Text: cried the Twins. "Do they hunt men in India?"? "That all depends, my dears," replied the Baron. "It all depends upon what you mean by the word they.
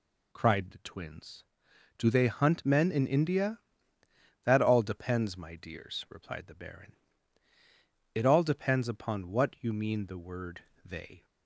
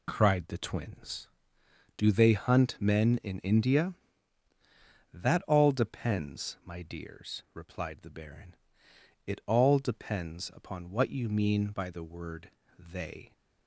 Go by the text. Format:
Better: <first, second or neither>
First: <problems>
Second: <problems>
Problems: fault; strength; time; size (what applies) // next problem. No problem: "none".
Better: second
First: skips "by"; at 10.0 s // pauses between "word" and "they"; slight; at 10.6 s; 0.22 s long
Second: pauses between "word" and "they"; slight; at 12.5 s; 0.26 s long